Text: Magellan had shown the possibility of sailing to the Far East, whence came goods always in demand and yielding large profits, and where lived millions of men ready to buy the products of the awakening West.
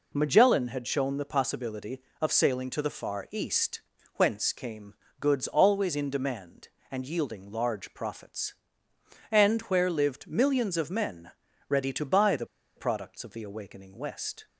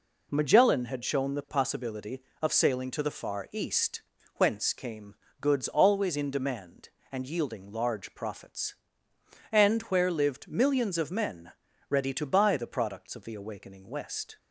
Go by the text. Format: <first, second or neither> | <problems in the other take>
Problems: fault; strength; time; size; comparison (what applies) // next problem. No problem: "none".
second | pauses between "came" and "goods"; slight; at 4.9 s; 0.26 s long; slight in the second // pauses between "men" and "ready"; slight; at 11.3 s; 0.36 s long; slight in the second // pauses between "the" and "products"; slight; at 12.4 s; 0.31 s long